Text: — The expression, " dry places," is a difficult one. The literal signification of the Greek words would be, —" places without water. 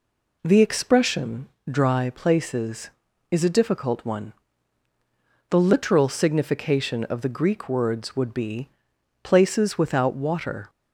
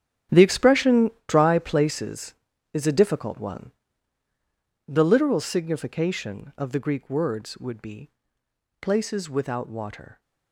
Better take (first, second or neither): first